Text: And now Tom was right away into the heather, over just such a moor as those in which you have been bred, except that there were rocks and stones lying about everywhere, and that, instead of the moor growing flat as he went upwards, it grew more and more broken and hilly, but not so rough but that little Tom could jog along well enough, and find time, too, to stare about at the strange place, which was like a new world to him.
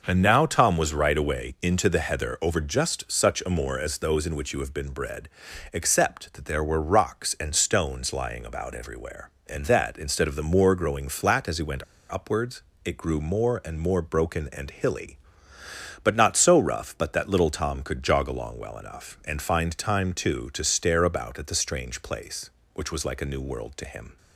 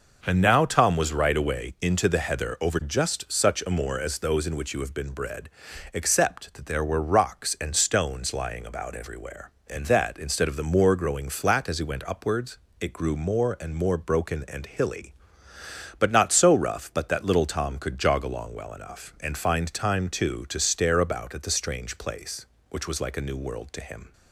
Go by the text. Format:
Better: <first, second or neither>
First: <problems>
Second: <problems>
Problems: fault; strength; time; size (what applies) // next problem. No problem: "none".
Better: second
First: pauses between "went" and "upwards"; slight; at 11.8 s; 0.26 s long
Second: none